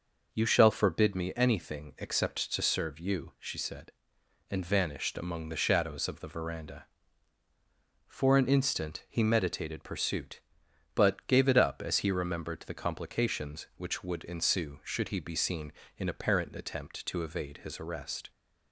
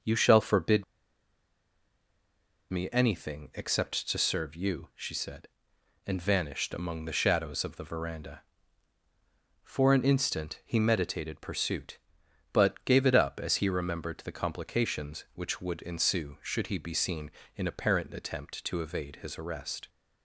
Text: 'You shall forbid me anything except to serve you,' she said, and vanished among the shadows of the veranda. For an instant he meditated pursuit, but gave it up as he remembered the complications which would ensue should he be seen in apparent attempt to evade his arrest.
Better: first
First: none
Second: pauses between "forbid" and "me"; strong; at 0.8 s; 1.8 s long

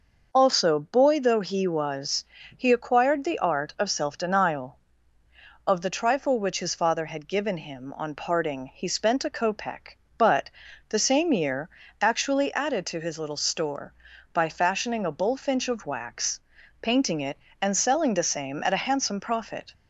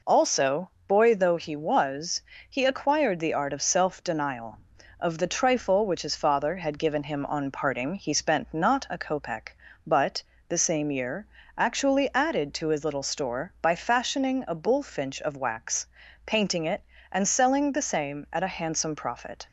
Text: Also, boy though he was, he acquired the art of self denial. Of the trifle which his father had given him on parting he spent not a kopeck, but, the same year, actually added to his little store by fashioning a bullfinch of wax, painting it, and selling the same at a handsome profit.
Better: second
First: skips "not"; at 9.2 s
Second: none

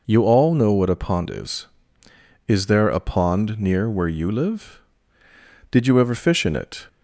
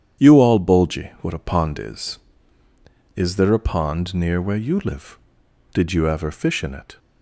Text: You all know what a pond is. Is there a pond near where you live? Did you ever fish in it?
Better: first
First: none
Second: starts louder than the rest; strong; until 1.2 s; 9 dB // says "bulgy" for "know"; at 0.5 s

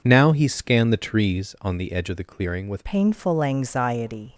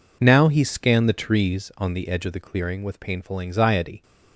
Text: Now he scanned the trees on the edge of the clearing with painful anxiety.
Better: second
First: changes voice at "painful"; from 2.8 s on; 1.5 s long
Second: none

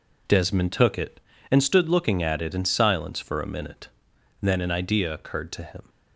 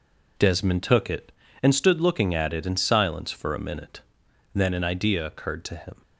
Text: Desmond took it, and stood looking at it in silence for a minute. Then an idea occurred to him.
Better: neither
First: none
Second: none

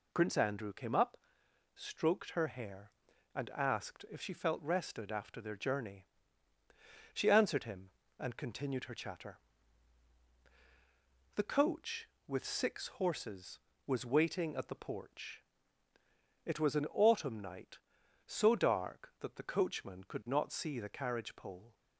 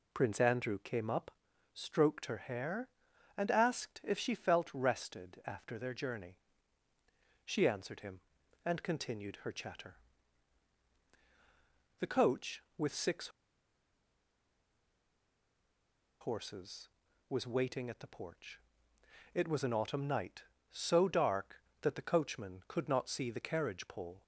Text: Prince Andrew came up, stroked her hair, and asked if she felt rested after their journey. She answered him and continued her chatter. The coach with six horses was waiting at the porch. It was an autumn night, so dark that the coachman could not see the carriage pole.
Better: first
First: none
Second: pauses between "six" and "horses"; strong; at 13.2 s; 2.9 s long

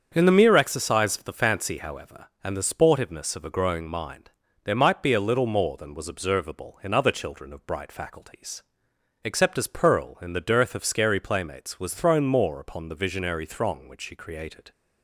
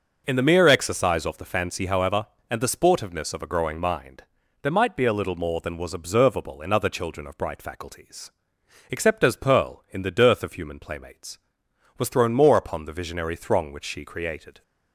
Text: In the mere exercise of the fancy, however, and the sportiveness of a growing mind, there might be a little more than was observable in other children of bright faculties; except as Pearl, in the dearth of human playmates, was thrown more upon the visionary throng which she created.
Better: second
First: starts louder than the rest; strong; until 1.1 s; 7.5 dB // says "scary" for "human"; at 10.8 s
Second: none

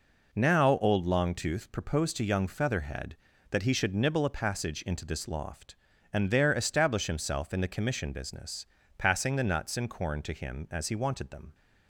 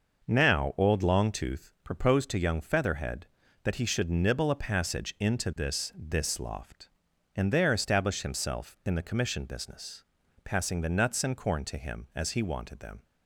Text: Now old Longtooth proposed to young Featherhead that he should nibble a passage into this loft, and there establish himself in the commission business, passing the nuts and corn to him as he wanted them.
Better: first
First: none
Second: says "this" twice; at 5.9 s

